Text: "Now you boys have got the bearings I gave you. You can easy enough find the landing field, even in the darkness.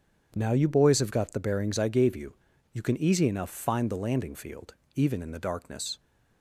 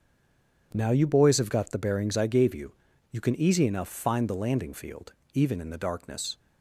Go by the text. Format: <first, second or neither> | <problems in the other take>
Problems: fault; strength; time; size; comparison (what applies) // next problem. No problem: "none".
first | stays silent before the first word; slight; until 0.7 s; 0.7 s long // starts louder than the rest; strong; until 1.7 s; 7.5 dB; strong in the first